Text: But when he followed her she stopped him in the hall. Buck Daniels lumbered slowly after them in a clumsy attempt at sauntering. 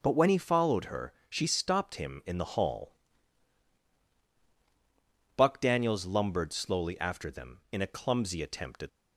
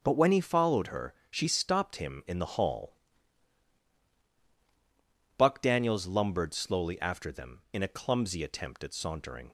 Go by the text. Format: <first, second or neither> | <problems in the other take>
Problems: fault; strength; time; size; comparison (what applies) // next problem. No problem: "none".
second | pauses between "her" and "she"; slight; at 1.1 s; 0.16 s long; slight in the second // stops before "sauntering"; at 8.8 s